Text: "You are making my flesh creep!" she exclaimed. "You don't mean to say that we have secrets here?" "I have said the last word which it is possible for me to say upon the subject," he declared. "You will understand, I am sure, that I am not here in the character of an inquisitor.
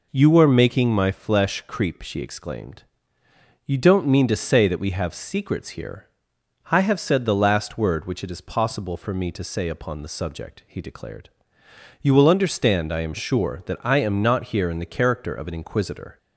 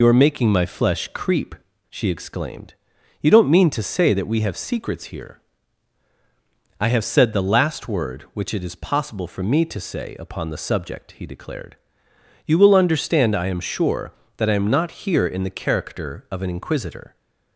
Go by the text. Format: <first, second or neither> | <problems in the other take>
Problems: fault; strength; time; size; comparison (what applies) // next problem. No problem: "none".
first | loses the start of "You"; at 0.0 s; 55 ms